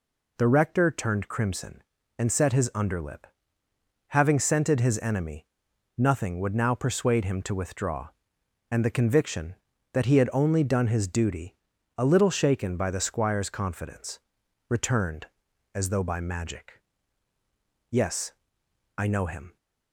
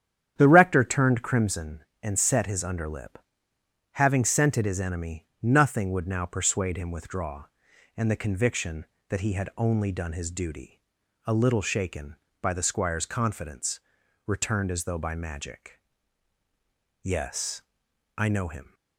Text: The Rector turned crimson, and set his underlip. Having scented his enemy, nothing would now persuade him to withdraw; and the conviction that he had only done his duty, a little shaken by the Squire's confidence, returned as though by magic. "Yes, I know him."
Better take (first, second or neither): first